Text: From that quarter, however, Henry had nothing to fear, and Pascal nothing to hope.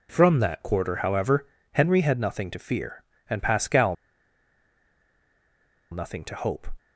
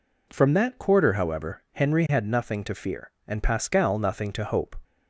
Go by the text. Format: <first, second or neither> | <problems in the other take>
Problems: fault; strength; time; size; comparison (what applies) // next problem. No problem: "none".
second | pauses between "Pascal" and "nothing"; strong; at 3.9 s; 1.9 s long